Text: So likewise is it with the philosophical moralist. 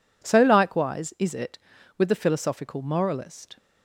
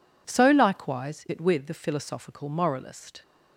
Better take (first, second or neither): first